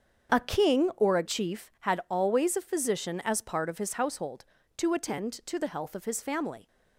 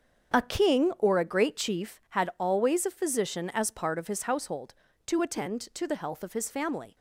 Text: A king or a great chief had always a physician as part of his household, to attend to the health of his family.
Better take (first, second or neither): second